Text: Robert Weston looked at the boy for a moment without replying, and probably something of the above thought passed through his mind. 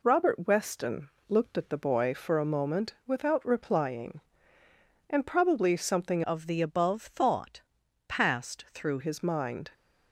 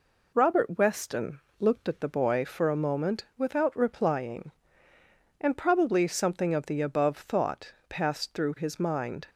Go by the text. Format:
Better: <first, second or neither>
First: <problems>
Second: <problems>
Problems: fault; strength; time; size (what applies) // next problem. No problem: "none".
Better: second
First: pauses between "Weston" and "looked"; slight; at 1.0 s; 0.18 s long // changes voice from "of" to "through"; from 6.2 to 8.9 s; 2.7 s long // pauses between "thought" and "passed"; noticeable; at 7.6 s; 0.48 s long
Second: pauses between "Weston" and "looked"; slight; at 1.4 s; 0.18 s long // pauses between "thought" and "passed"; slight; at 7.7 s; 0.16 s long